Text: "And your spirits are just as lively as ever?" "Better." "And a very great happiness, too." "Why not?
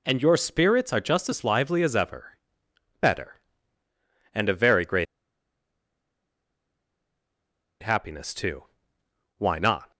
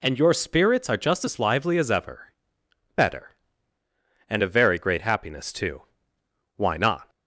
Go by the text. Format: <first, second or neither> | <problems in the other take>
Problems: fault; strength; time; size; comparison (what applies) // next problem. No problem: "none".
second | pauses between "great" and "happiness"; strong; at 5.0 s; 2.7 s long